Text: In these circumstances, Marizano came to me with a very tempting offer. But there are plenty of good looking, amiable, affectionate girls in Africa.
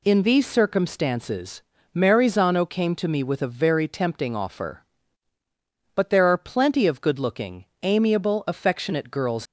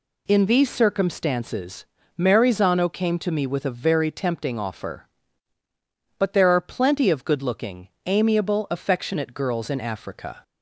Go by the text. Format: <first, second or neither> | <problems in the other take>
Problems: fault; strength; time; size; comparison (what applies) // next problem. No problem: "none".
second | stops before "in Africa"; at 9.4 s